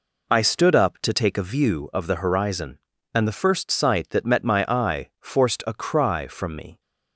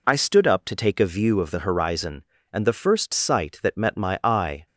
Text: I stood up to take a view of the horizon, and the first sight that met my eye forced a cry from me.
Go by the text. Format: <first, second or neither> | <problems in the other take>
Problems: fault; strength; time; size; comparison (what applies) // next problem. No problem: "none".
first | stops before "forced a cry from me"; at 4.6 s